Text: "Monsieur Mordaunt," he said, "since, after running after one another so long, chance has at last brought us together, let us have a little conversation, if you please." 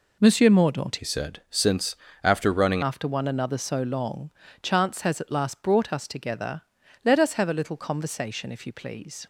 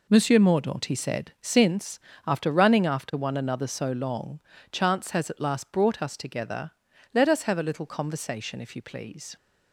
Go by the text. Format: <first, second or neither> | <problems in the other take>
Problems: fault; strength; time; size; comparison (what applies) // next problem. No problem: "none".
second | changes voice from "he" to "running"; from 0.9 to 2.8 s; 1.9 s long